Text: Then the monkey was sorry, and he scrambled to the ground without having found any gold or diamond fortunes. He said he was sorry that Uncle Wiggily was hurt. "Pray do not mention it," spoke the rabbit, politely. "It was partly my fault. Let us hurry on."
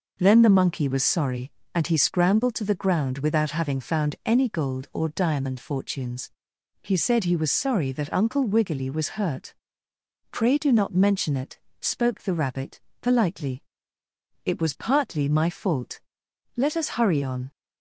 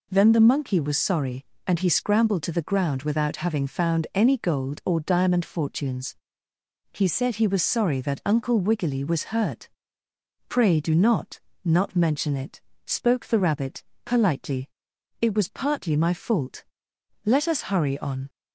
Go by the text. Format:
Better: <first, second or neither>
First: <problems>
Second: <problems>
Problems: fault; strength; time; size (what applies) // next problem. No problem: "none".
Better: first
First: none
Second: says "not" twice; at 11.6 s